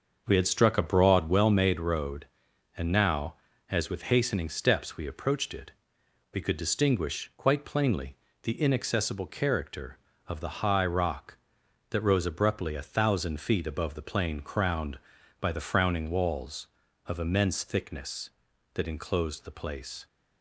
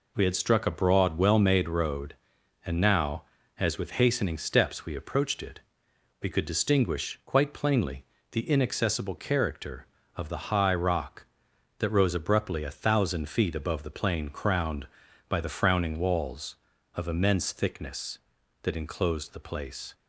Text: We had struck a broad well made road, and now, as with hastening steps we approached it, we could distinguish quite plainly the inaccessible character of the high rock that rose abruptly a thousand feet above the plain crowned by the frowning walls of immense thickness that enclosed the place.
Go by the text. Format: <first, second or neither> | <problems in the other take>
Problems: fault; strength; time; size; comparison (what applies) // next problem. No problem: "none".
second | starts louder than the rest; until 1.4 s; 6.5 dB // pauses between "plainly" and "the"; slight; at 8.1 s; 0.28 s long; slight in the second